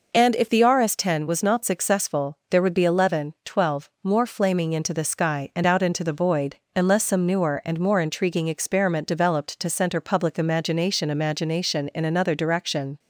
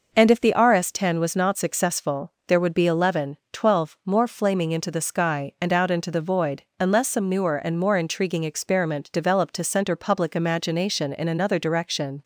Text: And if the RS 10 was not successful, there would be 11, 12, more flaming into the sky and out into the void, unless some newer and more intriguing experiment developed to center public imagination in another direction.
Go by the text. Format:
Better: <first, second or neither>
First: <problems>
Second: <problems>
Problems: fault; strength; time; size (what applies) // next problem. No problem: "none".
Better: second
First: says "imagination" twice; at 11.1 s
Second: none